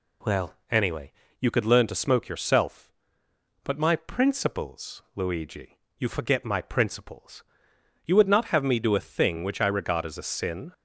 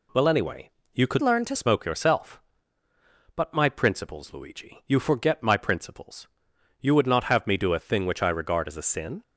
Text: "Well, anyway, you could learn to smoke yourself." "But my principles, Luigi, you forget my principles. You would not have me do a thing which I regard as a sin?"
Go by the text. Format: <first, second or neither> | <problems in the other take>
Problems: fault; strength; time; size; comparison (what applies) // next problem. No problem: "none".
first | changes voice from "learn" to "to"; from 1.2 to 1.5 s; 0.3 s long